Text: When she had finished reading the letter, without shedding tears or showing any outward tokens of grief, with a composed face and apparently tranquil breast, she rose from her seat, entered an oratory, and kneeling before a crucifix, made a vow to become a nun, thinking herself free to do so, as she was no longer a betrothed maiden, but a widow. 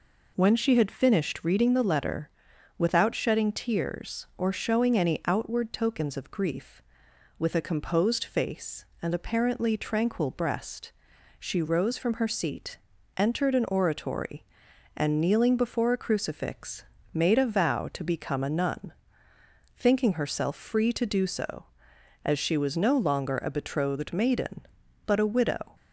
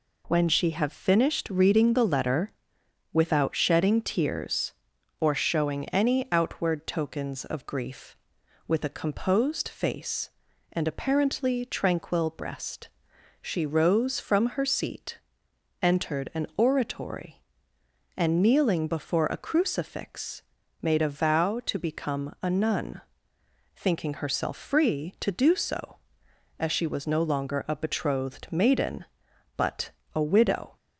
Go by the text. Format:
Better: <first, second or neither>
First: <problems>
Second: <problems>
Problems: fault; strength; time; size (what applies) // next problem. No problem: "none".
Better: first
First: none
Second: says "have" for "had"; at 0.7 s // pauses between "but" and "a"; slight; at 29.9 s; 0.22 s long